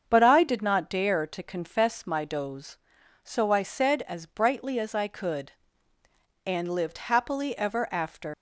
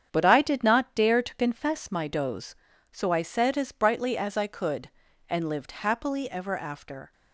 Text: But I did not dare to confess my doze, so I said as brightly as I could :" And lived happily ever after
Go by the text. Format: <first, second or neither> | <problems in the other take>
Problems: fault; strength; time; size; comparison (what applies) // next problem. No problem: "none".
second | starts louder than the rest; strong; until 1.0 s; 7.5 dB; strong in the second // leaves "after" unfinished; at 8.3 s; 105 ms